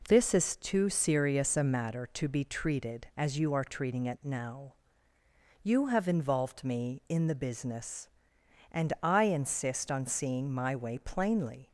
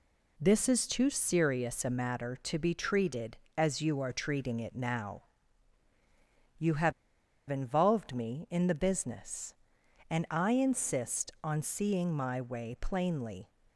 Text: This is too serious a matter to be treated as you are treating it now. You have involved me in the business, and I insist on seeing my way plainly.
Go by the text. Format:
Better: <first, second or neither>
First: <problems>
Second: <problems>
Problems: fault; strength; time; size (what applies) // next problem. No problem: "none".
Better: first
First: none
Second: pauses between "have" and "involved"; noticeable; at 6.9 s; 0.57 s long